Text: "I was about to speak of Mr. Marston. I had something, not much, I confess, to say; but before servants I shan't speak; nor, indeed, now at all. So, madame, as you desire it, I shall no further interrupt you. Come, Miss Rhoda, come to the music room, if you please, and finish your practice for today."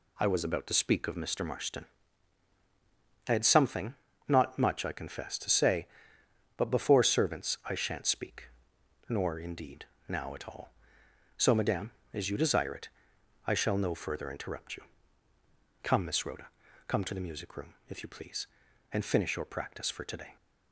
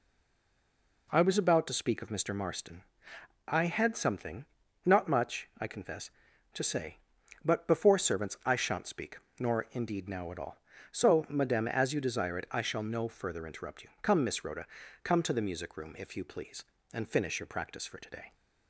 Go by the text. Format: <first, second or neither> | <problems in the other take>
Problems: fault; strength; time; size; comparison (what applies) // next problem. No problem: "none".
first | stays silent before the first word; until 1.0 s; 1.0 s long